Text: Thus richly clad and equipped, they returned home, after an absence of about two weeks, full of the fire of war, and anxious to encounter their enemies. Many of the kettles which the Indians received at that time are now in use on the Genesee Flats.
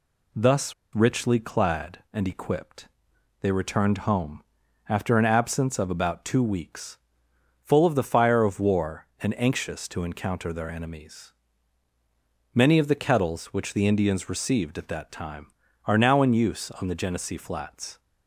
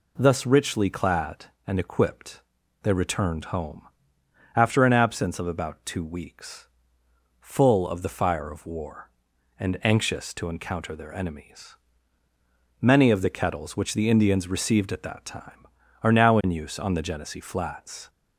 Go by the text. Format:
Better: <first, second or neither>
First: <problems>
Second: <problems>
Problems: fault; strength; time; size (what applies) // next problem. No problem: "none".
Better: second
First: pauses between "Thus" and "richly"; slight; at 0.7 s; 0.23 s long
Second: none